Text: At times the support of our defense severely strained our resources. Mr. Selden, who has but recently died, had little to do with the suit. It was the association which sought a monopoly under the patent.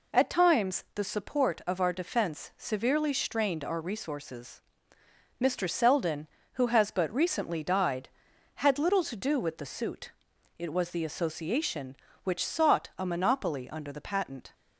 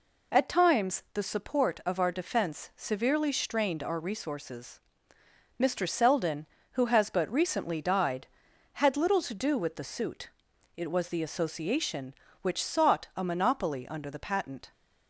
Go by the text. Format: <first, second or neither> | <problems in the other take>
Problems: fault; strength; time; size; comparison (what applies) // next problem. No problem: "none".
neither | none